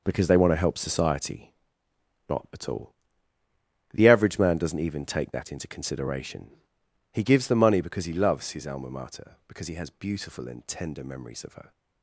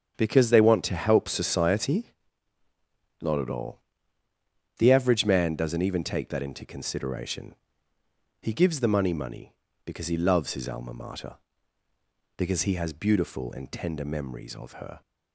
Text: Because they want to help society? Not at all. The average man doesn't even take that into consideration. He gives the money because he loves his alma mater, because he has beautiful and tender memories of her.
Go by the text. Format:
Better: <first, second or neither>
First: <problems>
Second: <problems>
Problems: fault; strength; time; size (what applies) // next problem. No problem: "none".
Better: first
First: none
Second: starts louder than the rest; strong; until 1.1 s; 8 dB // says "money" twice; at 9.1 s